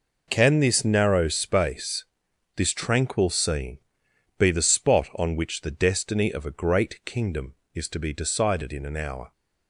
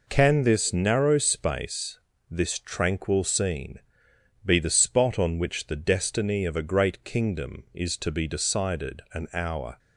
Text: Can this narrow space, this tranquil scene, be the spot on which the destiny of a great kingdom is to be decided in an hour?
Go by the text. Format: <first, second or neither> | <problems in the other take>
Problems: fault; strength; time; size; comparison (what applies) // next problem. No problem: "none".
first | skips "in"; at 9.0 s